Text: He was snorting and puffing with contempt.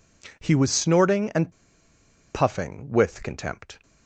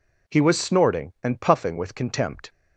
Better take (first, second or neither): second